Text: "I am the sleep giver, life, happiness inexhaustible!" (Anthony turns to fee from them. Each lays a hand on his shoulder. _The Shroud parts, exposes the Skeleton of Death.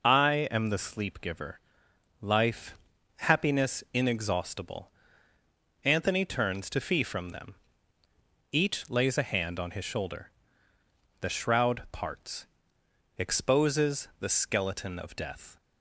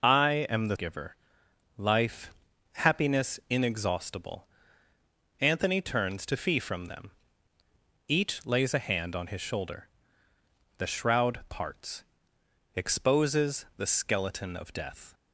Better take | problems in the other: first | skips "sleep"; at 0.7 s

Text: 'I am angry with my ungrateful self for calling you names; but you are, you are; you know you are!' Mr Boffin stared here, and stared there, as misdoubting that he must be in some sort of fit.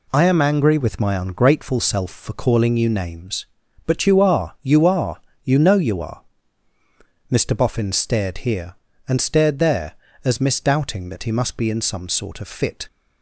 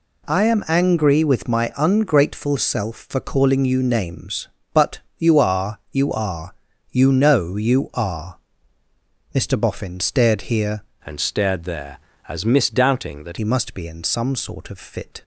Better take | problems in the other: first | pauses between "but" and "you"; slight; at 5.0 s; 0.18 s long // changes voice from "and" to "that"; from 11.0 to 13.3 s; 2.3 s long

